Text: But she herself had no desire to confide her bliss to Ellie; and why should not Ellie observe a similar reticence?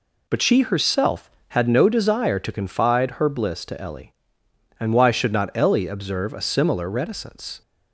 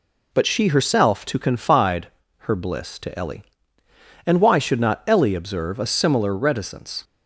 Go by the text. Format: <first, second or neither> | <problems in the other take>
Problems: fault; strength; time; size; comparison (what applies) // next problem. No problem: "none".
first | skips "had no desire"; at 1.2 s // pauses between "confide" and "her"; at 2.0 s; 0.38 s long